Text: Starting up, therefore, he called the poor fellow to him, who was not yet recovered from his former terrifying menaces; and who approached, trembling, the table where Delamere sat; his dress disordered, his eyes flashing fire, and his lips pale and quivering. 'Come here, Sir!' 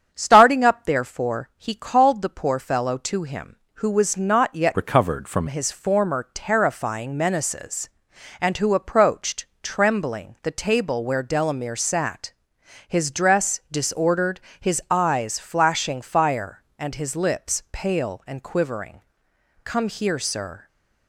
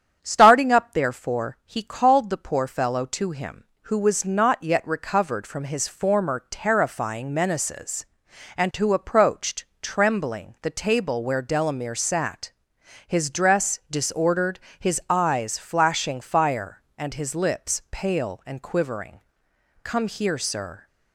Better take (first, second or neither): second